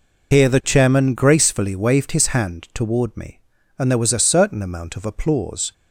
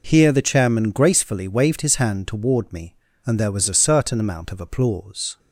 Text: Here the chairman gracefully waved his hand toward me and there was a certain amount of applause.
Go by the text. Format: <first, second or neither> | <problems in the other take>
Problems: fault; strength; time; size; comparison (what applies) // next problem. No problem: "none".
second | loses the start of "Here"; at 0.3 s; 60 ms